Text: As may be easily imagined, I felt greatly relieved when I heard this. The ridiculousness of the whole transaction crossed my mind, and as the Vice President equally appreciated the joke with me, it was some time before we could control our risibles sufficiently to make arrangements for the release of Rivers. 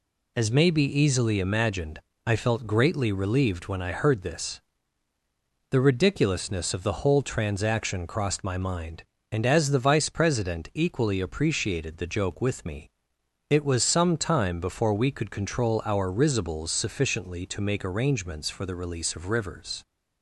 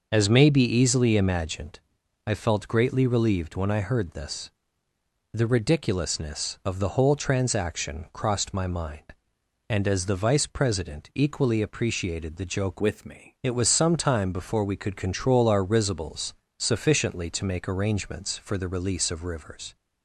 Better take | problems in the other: first | changes voice from "with" to "me"; from 12.7 to 13.3 s; 0.6 s long // pauses between "risibles" and "sufficiently"; slight; at 16.3 s; 0.24 s long

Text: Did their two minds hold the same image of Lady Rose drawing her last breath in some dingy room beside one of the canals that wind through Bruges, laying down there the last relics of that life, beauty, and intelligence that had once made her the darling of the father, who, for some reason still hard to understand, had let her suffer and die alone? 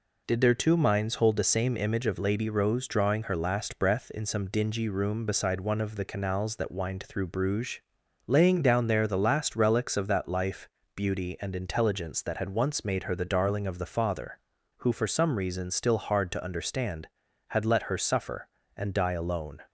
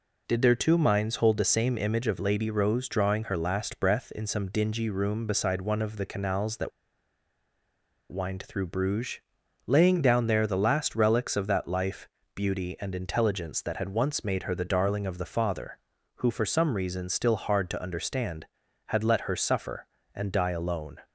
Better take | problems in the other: first | pauses between "that" and "wind"; strong; at 6.7 s; 1.4 s long

